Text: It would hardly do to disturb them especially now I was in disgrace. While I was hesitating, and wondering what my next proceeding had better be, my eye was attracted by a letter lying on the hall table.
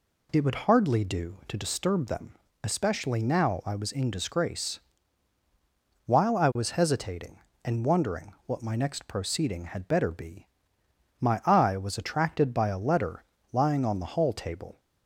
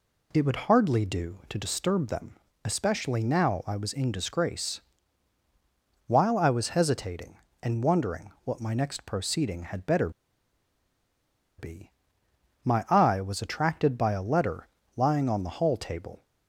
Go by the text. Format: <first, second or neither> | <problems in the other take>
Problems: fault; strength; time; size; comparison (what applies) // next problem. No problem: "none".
first | pauses between "them" and "especially"; slight; at 2.3 s; 0.28 s long; slight in the first // pauses between "better" and "be"; strong; at 10.0 s; 1.4 s long // pauses between "letter" and "lying"; slight; at 14.6 s; 0.26 s long; slight in the first